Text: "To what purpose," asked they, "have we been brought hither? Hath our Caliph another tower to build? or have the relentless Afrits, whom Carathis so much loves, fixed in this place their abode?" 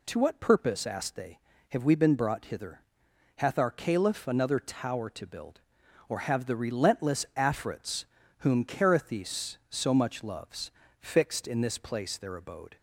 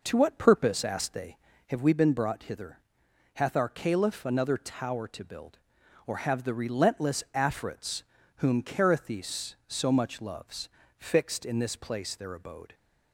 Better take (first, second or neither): first